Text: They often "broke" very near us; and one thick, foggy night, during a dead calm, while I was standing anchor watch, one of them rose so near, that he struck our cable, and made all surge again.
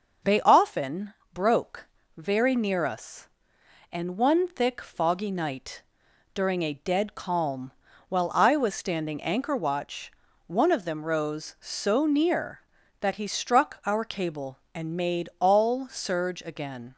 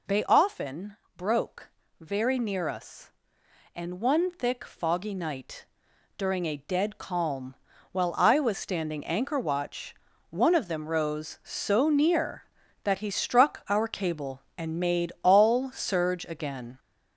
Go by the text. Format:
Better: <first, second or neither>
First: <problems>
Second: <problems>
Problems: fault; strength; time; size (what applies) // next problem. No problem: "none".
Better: first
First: pauses between "often" and "broke"; slight; at 1.1 s; 0.20 s long // pauses between "broke" and "very"; slight; at 1.8 s; 0.30 s long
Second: gets louder; noticeable; throughout; 5 dB // pauses between "often" and "broke"; slight; at 0.9 s; 0.20 s long // pauses between "broke" and "very"; slight; at 1.6 s; 0.30 s long